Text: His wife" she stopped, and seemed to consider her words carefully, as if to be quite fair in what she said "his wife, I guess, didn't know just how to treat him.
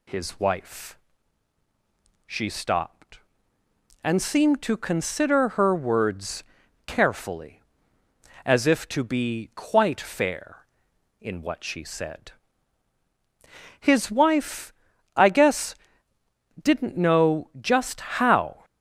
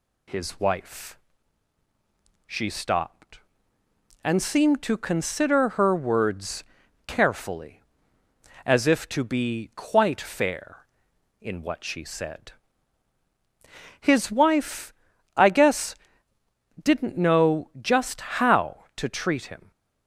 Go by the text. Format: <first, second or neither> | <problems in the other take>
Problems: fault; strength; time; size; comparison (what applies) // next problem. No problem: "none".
second | pauses between "wife" and "she"; strong; at 0.9 s; 1.2 s long; strong in the second // pauses between "words" and "carefully"; at 6.4 s; 0.44 s long; also in the second // pauses between "said" and "his"; strong; at 12.3 s; 1.4 s long; strong in the second // pauses between "just" and "how"; slight; at 18.0 s; 0.16 s long; slight in the second // stops before "to treat him"; at 18.6 s